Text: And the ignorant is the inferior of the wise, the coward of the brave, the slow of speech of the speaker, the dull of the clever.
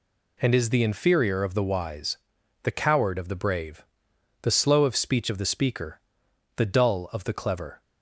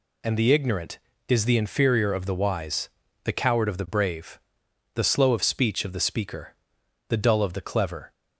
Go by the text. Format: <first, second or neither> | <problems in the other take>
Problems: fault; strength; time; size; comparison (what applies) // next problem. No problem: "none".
second | skips "the ignorant"; at 0.5 s